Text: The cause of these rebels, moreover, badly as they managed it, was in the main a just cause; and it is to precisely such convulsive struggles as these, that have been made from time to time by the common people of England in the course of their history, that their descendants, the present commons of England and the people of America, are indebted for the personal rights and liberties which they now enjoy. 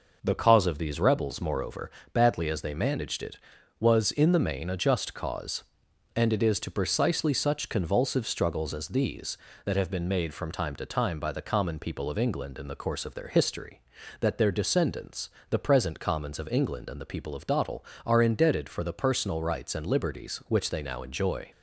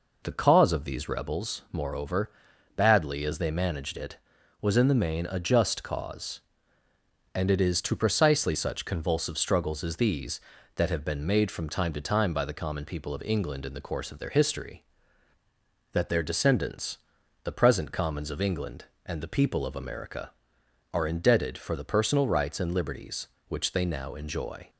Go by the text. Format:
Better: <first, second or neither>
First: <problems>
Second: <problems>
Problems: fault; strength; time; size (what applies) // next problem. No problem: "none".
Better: second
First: says "Dottle" for "America"; at 17.4 s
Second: none